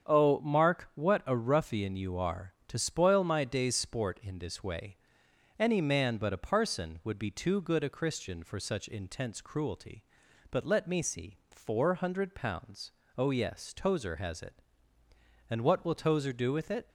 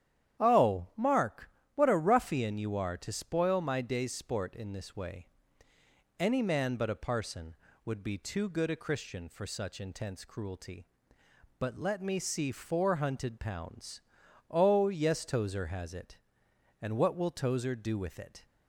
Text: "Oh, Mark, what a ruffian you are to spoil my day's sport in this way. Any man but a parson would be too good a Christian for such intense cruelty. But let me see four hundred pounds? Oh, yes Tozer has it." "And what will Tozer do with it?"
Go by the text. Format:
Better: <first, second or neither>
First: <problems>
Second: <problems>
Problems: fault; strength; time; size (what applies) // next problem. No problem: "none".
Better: first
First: starts louder than the rest; strong; until 1.1 s; 8 dB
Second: starts louder than the rest; strong; until 1.4 s; 10 dB // says "hunted" for "hundred"; at 12.9 s